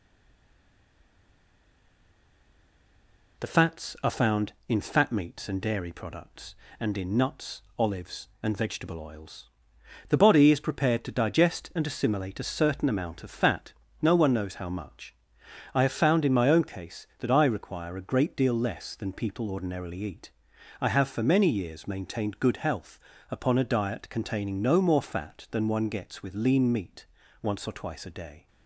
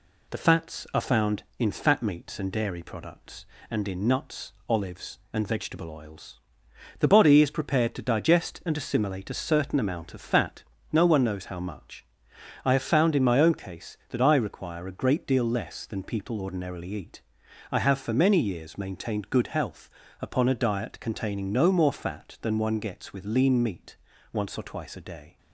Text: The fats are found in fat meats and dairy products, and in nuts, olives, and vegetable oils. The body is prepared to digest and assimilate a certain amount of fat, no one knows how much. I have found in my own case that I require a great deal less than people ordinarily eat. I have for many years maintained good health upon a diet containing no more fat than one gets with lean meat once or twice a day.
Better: second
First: stays silent before the first word; strong; until 3.3 s; 3.3 s long // pauses between "health" and "upon"; slight; at 22.9 s; 0.30 s long // pauses between "meat" and "once"; at 27.0 s; 0.38 s long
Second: pauses between "health" and "upon"; slight; at 19.8 s; 0.30 s long // pauses between "meat" and "once"; at 23.9 s; 0.38 s long

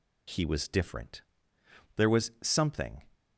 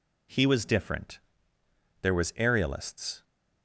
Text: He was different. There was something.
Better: first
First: none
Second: says "aerialists" for "something"; at 2.3 s

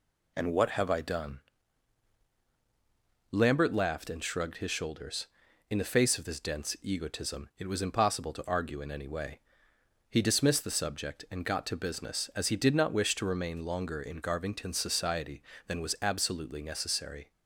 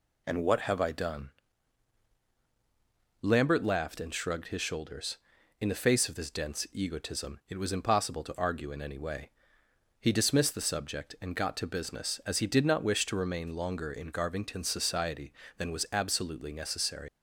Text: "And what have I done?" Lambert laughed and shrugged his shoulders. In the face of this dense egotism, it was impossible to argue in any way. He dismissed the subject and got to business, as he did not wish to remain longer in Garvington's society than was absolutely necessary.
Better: first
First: none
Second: leaves "necessary" unfinished; at 17.0 s; 135 ms

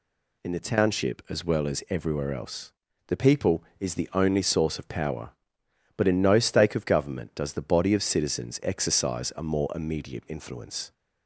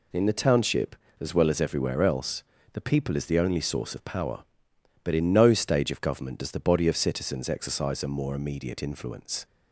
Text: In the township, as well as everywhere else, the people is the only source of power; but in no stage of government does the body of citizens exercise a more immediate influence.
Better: second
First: says "stake" for "stage"; at 6.3 s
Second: none

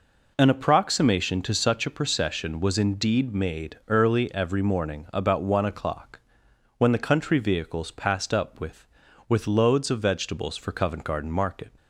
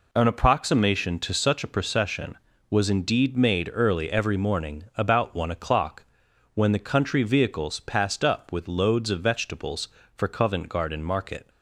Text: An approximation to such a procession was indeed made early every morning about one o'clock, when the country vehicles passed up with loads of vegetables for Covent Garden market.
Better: second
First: says "with" twice; at 9.2 s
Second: none

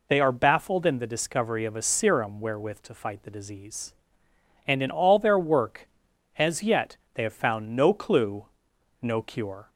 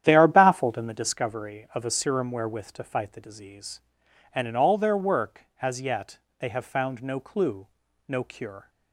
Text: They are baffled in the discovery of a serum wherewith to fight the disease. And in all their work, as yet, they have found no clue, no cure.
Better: first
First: none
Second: starts louder than the rest; strong; until 1.2 s; 10.5 dB

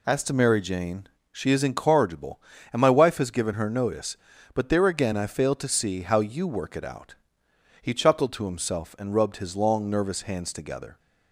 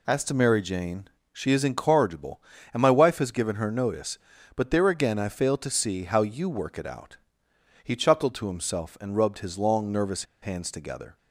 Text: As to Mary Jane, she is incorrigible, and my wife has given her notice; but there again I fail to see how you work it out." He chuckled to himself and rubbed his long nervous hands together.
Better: first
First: none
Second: pauses between "nervous" and "hands"; slight; at 10.2 s; 0.17 s long

